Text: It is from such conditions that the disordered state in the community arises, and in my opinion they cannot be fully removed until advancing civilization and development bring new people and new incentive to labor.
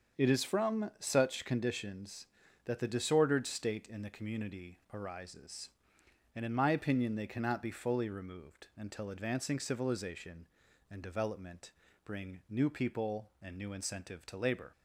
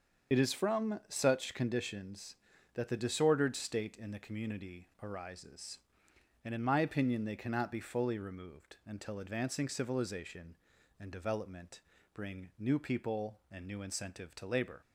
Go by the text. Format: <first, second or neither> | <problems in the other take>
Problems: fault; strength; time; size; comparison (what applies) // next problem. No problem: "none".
first | loses the start of "It"; at 0.3 s; 40 ms // starts louder than the rest; until 1.3 s; 7 dB; also in the first // pauses between "development" and "bring"; slight; at 11.8 s; 0.34 s long; slight in the first